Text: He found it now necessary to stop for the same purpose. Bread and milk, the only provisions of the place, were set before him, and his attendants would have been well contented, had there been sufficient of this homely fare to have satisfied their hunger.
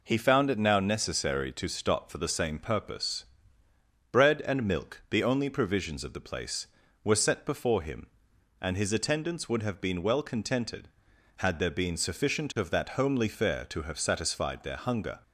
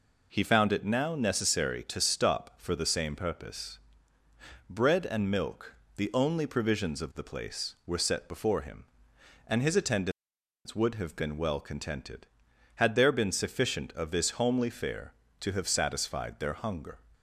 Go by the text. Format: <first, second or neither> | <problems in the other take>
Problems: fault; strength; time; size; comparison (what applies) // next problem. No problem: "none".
second | says "that" for "this"; at 12.6 s